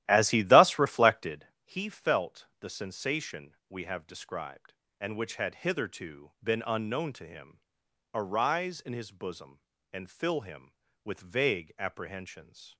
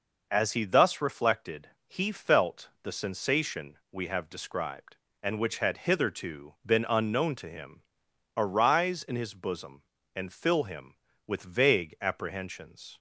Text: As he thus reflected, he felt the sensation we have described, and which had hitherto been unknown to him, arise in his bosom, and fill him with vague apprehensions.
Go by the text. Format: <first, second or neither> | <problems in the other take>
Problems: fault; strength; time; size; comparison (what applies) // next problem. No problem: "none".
second | starts louder than the rest; strong; until 1.5 s; 13.5 dB